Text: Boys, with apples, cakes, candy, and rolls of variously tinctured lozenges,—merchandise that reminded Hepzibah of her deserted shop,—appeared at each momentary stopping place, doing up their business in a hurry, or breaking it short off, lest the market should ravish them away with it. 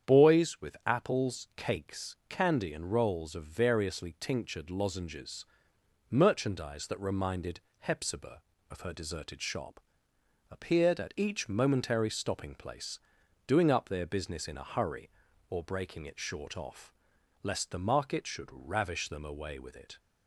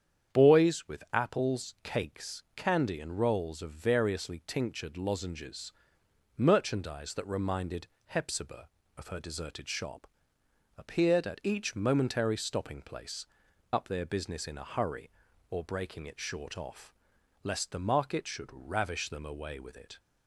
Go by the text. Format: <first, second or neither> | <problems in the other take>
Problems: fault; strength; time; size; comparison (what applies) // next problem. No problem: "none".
first | starts louder than the rest; strong; until 1.4 s; 8.5 dB; strong in the first // pauses between "reminded" and "Hepzibah"; slight; at 7.8 s; 0.18 s long; slight in the first // skips "doing"; at 13.4 s